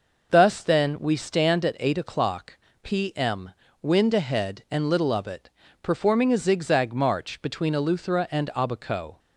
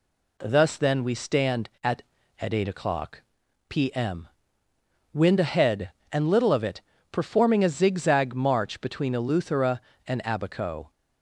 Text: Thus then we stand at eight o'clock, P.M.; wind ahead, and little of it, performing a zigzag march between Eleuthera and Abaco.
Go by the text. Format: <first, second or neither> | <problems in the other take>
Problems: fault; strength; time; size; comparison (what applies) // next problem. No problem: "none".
first | says "at" twice; at 2.4 s